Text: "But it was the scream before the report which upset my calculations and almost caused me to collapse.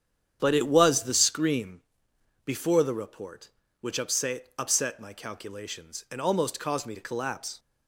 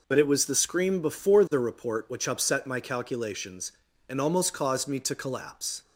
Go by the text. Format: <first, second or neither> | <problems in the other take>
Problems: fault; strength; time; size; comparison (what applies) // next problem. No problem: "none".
second | starts louder than the rest; strong; until 1.4 s; 9 dB // pauses between "scream" and "before"; noticeable; at 1.8 s; 0.66 s long // says "upset" twice; at 4.5 s